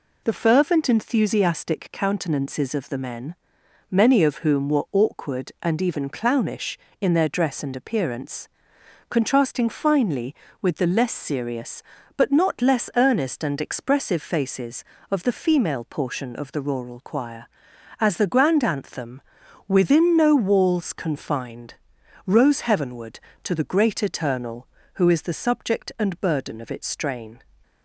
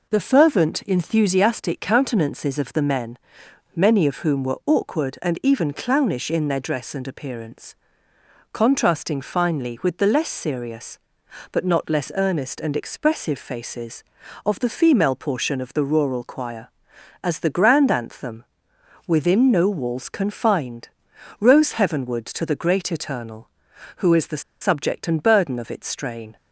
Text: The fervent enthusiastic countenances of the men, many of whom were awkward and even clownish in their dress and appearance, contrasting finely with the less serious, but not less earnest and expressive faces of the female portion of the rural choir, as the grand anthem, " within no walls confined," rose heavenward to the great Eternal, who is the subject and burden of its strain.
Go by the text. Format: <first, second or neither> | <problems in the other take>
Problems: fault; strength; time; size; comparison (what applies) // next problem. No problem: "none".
first | pauses between "the" and "subject"; slight; at 24.4 s; 0.18 s long